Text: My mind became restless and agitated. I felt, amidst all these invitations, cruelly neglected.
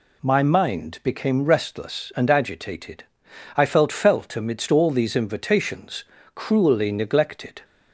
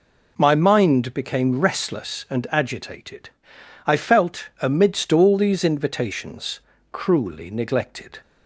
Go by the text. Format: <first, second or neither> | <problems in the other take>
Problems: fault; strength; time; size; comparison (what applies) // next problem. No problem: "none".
second | says "felt" twice; at 3.9 s